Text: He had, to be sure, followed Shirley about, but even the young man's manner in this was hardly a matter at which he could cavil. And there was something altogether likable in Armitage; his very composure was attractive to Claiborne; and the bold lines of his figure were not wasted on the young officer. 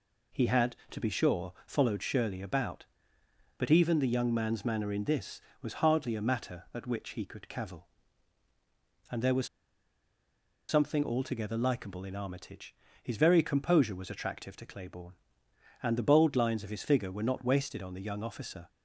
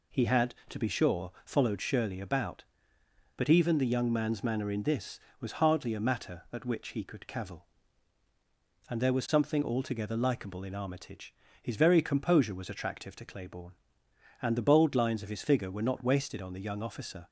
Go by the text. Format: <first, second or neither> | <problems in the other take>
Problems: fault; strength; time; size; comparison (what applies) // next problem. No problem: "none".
second | pauses between "was" and "something"; at 9.4 s; 1.2 s long